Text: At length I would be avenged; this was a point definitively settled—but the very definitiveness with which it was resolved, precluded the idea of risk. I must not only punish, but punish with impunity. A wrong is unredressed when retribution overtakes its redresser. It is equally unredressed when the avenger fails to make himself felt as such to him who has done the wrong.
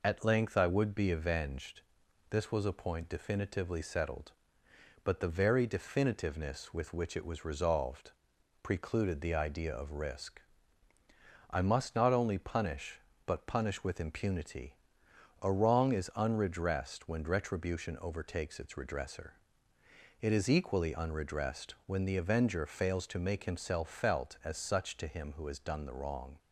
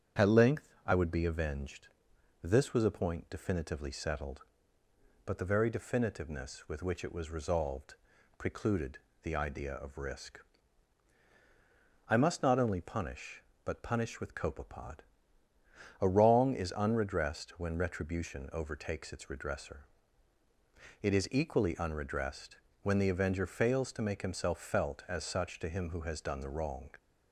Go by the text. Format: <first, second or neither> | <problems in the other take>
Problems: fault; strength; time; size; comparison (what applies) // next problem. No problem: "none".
first | starts louder than the rest; strong; until 1.3 s; 7.5 dB // pauses between "length" and "I"; slight; at 0.6 s; 0.20 s long // pauses between "precluded" and "the"; slight; at 8.9 s; 0.24 s long // says "copepod" for "impunity"; at 14.3 s // pauses between "unredressed" and "when"; slight; at 22.5 s; 0.28 s long